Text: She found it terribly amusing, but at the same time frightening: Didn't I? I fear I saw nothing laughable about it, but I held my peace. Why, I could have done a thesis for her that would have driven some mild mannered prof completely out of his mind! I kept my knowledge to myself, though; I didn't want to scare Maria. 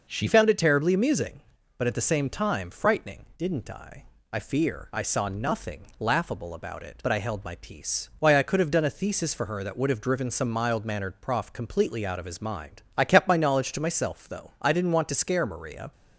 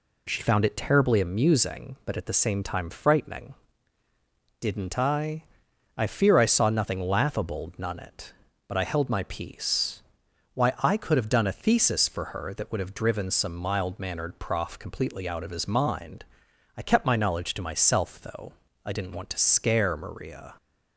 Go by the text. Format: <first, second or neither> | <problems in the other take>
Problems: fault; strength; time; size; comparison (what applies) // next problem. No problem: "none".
first | says "none" for "about"; at 7.7 s